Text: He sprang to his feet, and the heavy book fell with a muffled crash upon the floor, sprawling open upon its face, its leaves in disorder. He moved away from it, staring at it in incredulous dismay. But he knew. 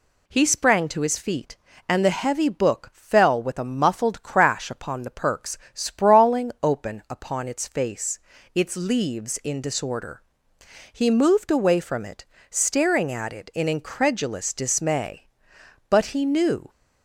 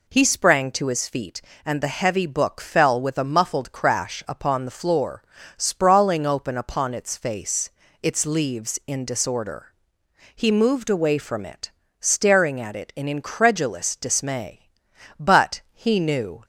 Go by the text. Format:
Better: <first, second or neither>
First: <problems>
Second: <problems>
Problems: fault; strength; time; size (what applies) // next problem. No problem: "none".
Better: second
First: says "perks" for "floor"; at 5.0 s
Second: none